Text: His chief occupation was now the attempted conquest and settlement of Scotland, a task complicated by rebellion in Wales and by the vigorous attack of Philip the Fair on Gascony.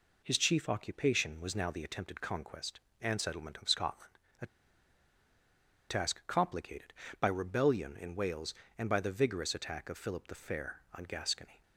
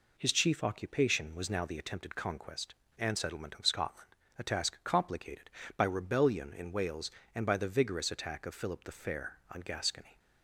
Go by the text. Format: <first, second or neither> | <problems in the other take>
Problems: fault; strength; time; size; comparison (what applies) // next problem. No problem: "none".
second | pauses between "a" and "task"; strong; at 4.4 s; 1.4 s long